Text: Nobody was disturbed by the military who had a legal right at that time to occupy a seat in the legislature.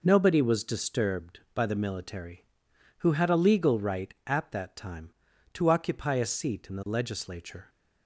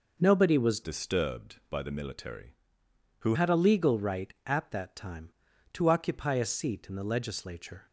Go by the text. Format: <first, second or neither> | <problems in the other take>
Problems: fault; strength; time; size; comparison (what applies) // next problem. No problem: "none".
first | changes voice from "disturbed" to "who"; from 0.8 to 3.3 s; 2.5 s long